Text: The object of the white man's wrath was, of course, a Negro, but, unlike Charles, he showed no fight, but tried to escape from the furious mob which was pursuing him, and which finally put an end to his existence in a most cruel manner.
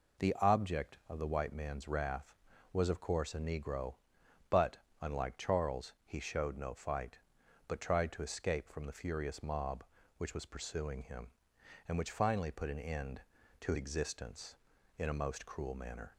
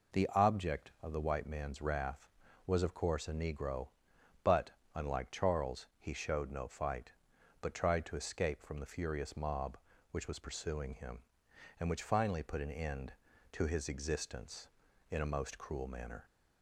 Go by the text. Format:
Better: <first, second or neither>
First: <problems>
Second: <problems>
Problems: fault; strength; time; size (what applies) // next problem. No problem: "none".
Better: second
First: skips "his"; at 13.7 s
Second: none